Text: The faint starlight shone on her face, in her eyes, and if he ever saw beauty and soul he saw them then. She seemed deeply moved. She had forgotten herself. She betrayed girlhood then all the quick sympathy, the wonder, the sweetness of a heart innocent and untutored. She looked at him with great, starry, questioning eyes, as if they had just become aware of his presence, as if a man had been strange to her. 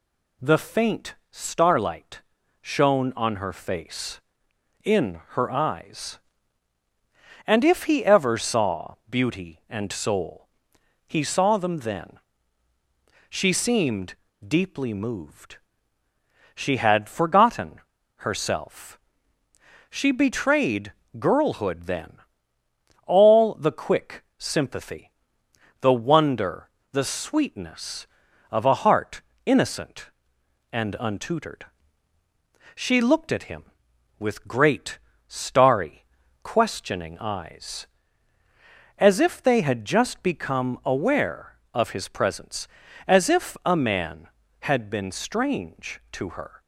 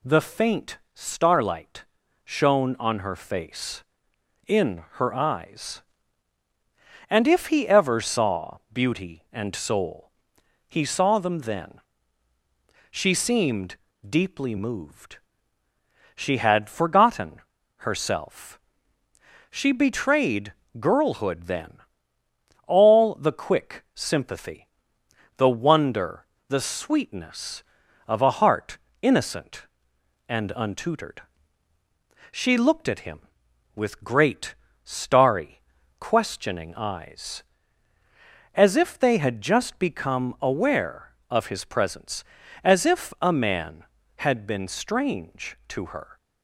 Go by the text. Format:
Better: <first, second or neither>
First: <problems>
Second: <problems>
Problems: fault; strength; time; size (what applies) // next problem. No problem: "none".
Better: neither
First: pauses between "starlight" and "shone"; at 2.2 s; 0.40 s long // pauses between "saw" and "beauty"; slight; at 8.9 s; 0.16 s long // pauses between "soul" and "he"; noticeable; at 10.4 s; 0.58 s long // pauses between "seemed" and "deeply"; slight; at 14.1 s; 0.32 s long // pauses between "forgotten" and "herself"; at 17.7 s; 0.38 s long // pauses between "betrayed" and "girlhood"; slight; at 20.9 s; 0.26 s long // pauses between "then" and "all"; noticeable; at 22.1 s; 0.92 s long // pauses between "heart" and "innocent"; slight; at 29.2 s; 0.24 s long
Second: pauses between "starlight" and "shone"; at 1.8 s; 0.40 s long // pauses between "saw" and "beauty"; slight; at 8.5 s; 0.16 s long // pauses between "soul" and "he"; noticeable; at 10.1 s; 0.56 s long // pauses between "seemed" and "deeply"; slight; at 13.7 s; 0.32 s long // pauses between "forgotten" and "herself"; at 17.4 s; 0.38 s long // pauses between "betrayed" and "girlhood"; slight; at 20.5 s; 0.26 s long // pauses between "then" and "all"; noticeable; at 21.7 s; 0.92 s long // pauses between "heart" and "innocent"; slight; at 28.7 s; 0.24 s long